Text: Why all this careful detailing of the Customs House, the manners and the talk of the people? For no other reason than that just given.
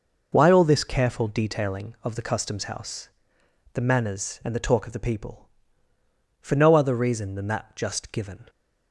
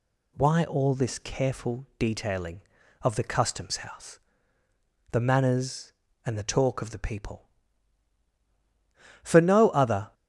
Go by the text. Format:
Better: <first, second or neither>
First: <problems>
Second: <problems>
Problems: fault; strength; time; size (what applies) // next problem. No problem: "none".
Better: first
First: none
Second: stops before "reason than that just given"; at 10.1 s